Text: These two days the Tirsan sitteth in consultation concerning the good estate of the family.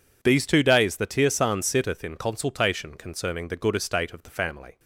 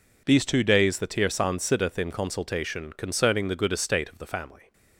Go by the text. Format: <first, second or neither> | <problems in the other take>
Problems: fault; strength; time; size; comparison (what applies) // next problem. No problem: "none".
neither | none